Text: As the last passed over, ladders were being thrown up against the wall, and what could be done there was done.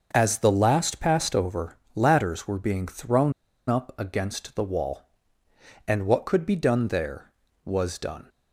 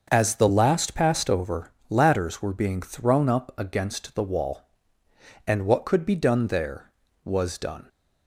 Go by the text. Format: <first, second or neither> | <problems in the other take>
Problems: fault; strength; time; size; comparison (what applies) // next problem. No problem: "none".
second | starts louder than the rest; until 1.1 s; 6 dB; also in the second // pauses between "thrown" and "up"; slight; at 3.3 s; 0.36 s long